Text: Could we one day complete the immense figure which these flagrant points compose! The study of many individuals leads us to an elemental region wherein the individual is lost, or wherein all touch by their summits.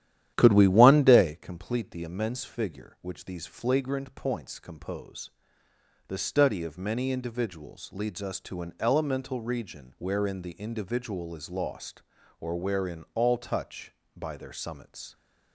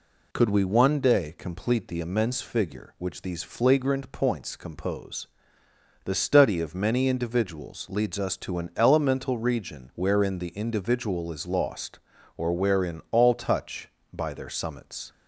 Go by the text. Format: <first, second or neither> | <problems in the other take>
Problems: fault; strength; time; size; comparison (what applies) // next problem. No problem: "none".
second | starts louder than the rest; strong; until 1.4 s; 11.5 dB